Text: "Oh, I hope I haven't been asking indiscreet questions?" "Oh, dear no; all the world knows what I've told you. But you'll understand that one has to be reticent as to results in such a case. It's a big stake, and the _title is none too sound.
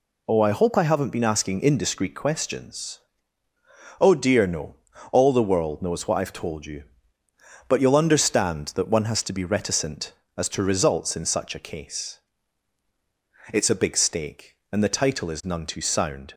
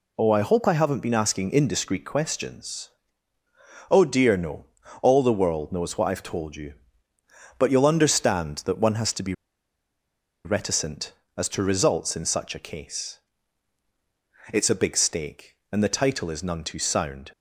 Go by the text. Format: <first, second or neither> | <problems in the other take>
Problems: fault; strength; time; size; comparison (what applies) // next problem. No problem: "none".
first | pauses between "be" and "reticent"; at 9.3 s; 1.1 s long